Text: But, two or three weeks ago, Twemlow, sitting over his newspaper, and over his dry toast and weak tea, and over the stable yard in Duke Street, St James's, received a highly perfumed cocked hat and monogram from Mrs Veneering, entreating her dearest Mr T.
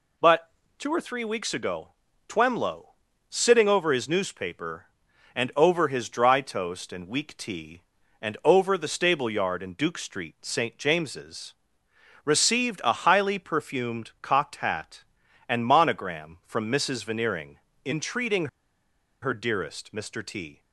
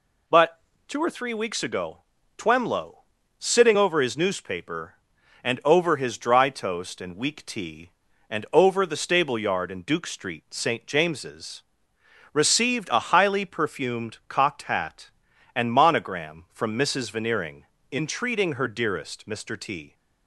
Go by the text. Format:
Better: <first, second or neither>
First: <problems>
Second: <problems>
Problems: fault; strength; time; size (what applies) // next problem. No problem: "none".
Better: second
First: pauses between "entreating" and "her"; noticeable; at 18.4 s; 0.75 s long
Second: none